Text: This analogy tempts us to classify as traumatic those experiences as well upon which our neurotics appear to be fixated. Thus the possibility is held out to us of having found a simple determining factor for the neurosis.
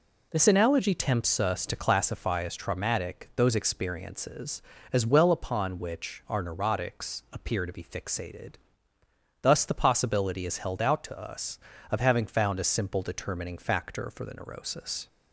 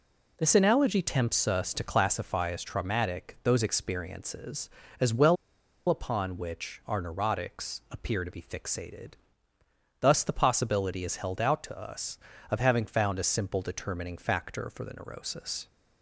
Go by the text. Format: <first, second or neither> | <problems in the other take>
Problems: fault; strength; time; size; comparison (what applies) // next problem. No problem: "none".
first | pauses between "well" and "upon"; noticeable; at 5.3 s; 0.53 s long